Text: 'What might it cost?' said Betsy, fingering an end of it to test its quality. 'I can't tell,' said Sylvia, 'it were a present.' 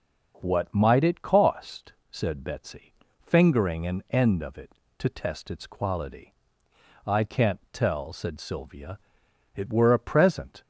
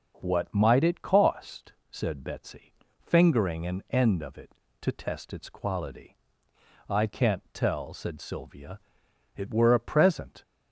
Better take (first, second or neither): neither